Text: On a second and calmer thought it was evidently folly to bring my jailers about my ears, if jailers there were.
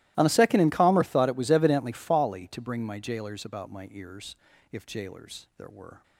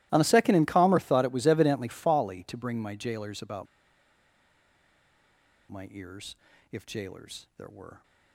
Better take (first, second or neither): first